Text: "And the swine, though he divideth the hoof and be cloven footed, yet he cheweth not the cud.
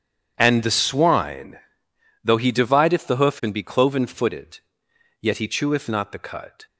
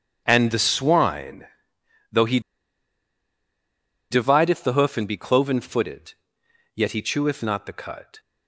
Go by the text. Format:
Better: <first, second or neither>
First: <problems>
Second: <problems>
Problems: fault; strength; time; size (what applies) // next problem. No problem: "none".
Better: first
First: starts louder than the rest; strong; until 1.3 s; 8.5 dB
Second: starts louder than the rest; strong; until 1.2 s; 8.5 dB // pauses between "he" and "divideth"; strong; at 2.3 s; 1.7 s long